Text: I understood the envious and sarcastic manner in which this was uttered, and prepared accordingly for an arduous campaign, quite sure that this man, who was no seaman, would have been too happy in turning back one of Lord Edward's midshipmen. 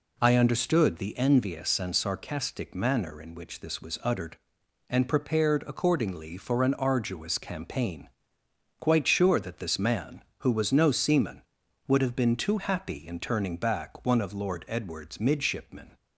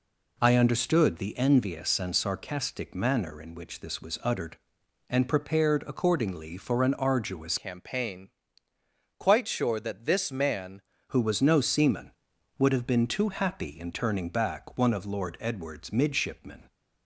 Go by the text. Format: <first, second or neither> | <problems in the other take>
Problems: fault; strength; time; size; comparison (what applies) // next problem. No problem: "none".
first | changes voice from "campaign" to "man"; from 7.5 to 10.8 s; 3.3 s long